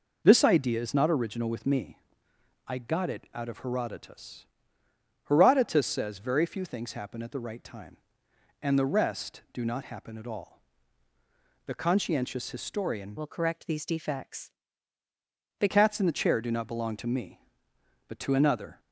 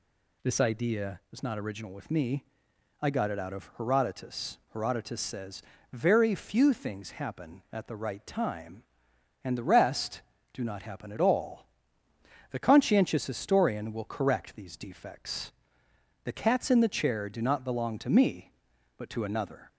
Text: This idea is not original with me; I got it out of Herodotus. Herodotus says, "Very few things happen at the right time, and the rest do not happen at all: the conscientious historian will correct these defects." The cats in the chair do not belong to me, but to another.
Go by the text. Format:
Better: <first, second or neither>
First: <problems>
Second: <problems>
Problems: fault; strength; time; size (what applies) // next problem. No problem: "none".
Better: second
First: changes voice from "will" to "The"; from 13.1 to 15.6 s; 2.5 s long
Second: none